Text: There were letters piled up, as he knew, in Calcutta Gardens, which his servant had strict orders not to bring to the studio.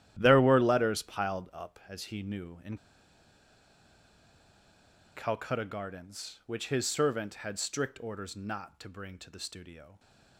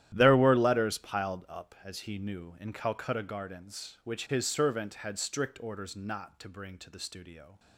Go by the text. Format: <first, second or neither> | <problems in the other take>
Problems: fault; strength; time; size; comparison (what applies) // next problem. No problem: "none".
second | starts louder than the rest; strong; until 1.2 s; 12 dB; strong in the second // pauses between "in" and "Calcutta"; strong; at 2.7 s; 2.4 s long